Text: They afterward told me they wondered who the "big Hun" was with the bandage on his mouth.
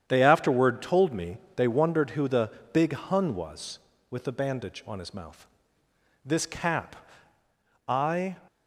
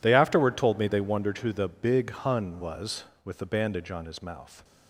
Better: second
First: starts louder than the rest; strong; until 1.1 s; 9 dB // pauses between "me" and "they"; slight; at 1.3 s; 0.18 s long // pauses between "the" and "big"; slight; at 2.5 s; 0.22 s long // goes on to say "This cap I"; strong; from 6.2 s on; 2.1 s long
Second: none

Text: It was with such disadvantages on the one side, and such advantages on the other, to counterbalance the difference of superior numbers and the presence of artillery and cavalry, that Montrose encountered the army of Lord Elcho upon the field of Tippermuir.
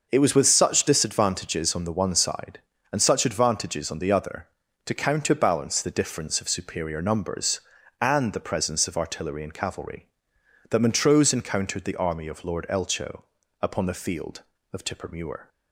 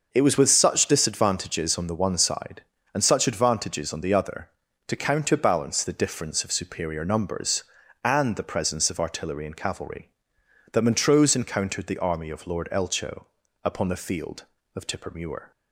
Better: neither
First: pauses between "Elcho" and "upon"; at 13.2 s; 0.38 s long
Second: pauses between "Elcho" and "upon"; at 13.2 s; 0.38 s long

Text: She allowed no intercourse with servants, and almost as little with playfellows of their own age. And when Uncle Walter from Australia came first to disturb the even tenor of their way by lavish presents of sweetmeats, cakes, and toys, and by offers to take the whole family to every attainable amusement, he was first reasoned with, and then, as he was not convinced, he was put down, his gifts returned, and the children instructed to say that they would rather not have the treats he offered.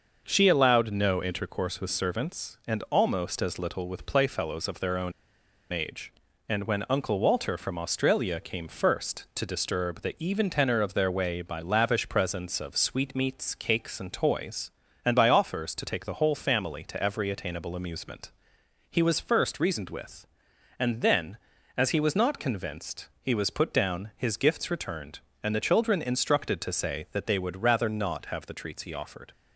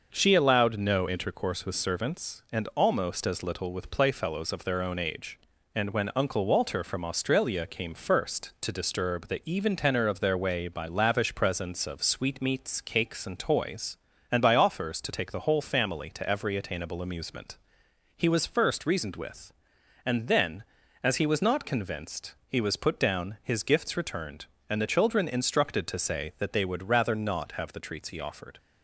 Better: second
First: starts louder than the rest; noticeable; until 1.2 s; 6 dB // pauses between "own" and "age"; noticeable; at 5.1 s; 0.59 s long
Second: starts louder than the rest; noticeable; until 1.1 s; 6 dB

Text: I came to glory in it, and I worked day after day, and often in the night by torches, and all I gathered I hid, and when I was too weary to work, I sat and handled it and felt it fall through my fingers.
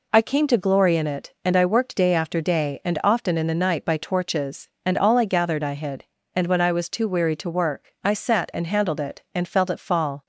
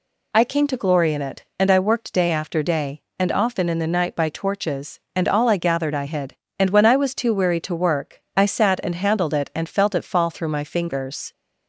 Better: second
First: stops before "through my fingers"; at 10.2 s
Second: none

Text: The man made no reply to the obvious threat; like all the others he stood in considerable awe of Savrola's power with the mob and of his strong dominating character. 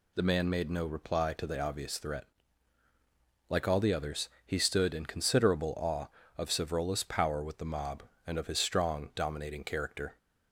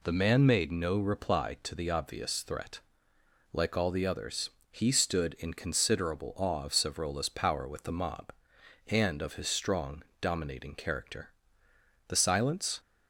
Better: first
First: pauses between "others" and "he"; slight; at 4.2 s; 0.18 s long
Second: pauses between "others" and "he"; slight; at 4.4 s; 0.22 s long // pauses between "strong" and "dominating"; slight; at 10.0 s; 0.18 s long // goes on to say "The silence"; noticeable; from 12.0 s on; 0.72 s long

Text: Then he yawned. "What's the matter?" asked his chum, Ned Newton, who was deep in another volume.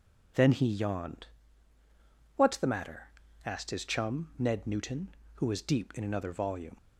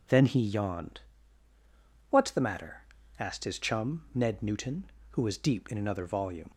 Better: neither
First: none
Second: none

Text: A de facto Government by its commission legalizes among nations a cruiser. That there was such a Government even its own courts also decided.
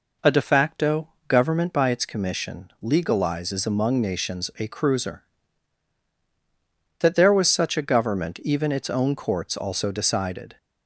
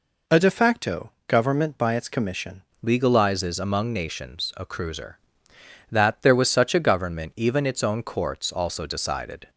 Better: first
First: pauses between "facto" and "Government"; slight; at 1.0 s; 0.18 s long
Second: pauses between "facto" and "Government"; slight; at 1.1 s; 0.16 s long // changes voice at "legalizes"; from 2.8 s on; 6.6 s long

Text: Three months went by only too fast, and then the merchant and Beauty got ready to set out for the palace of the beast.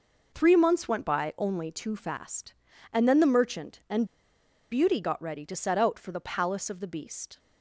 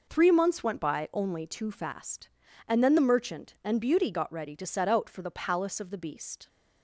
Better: second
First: pauses between "and" and "Beauty"; noticeable; at 4.0 s; 0.65 s long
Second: none

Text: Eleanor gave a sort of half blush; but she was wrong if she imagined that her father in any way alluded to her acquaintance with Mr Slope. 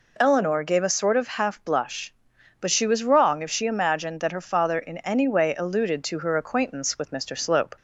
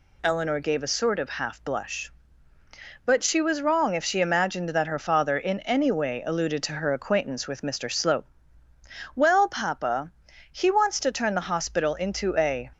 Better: first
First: none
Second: goes on to say "Well papa He wants to turn the hospital into a"; strong; from 9.1 s on; 3.5 s long

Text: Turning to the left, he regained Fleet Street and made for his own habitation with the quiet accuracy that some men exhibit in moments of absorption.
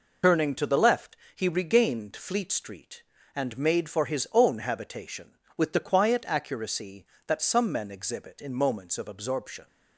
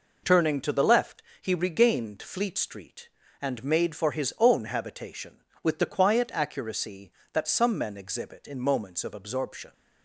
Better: second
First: loses the start of "Turning"; at 0.2 s; 50 ms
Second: none

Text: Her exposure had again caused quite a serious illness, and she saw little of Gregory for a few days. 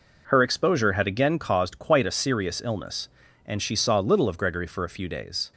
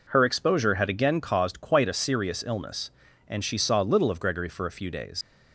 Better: first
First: none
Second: leaves "days" unfinished; at 5.2 s; 130 ms

